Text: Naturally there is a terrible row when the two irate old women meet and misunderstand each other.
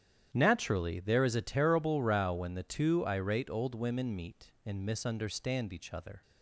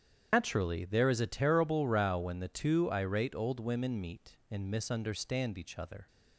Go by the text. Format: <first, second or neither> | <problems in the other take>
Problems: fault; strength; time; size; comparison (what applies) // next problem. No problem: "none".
first | loses the start of "Naturally"; at 0.3 s; 145 ms // starts louder than the rest; strong; until 1.3 s; 8.5 dB; strong in the first